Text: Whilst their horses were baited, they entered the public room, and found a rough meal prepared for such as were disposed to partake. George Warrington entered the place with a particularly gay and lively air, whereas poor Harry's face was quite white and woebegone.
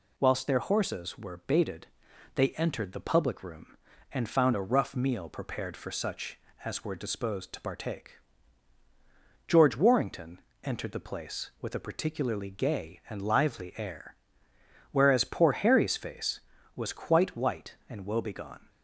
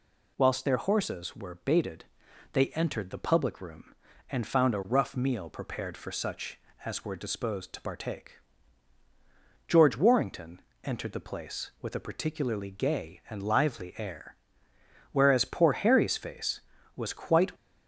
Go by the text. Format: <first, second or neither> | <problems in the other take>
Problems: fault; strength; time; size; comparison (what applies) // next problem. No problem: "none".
first | pauses between "Warrington" and "entered"; slight; at 10.5 s; 0.24 s long; slight in the first // stops before "white and woebegone"; at 17.5 s